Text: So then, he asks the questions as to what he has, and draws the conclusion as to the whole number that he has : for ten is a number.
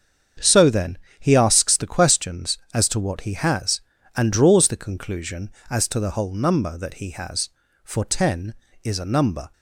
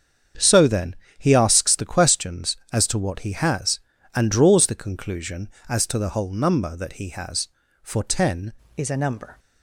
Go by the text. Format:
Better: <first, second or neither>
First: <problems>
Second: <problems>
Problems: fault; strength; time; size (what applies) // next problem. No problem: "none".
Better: first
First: starts louder than the rest; strong; until 1.6 s; 7.5 dB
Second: starts louder than the rest; strong; until 1.6 s; 7.5 dB // changes voice at "is"; from 8.7 s on; 0.6 s long